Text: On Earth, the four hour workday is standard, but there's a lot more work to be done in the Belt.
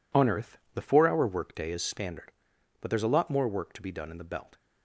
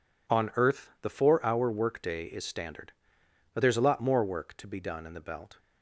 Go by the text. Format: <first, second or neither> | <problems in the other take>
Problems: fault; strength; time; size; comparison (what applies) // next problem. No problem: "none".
neither | none